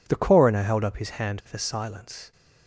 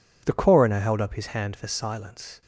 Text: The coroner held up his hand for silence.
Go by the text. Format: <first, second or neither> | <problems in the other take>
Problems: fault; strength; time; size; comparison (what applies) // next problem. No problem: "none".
neither | none